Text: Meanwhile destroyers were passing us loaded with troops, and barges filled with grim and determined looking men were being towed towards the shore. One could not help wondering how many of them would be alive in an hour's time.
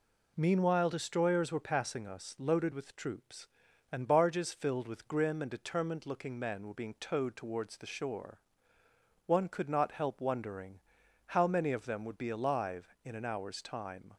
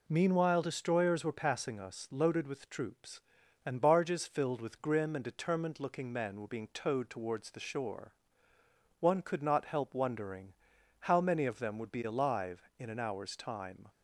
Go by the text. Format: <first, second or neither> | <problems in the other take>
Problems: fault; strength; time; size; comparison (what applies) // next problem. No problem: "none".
neither | pauses between "wondering" and "how"; noticeable; the same in both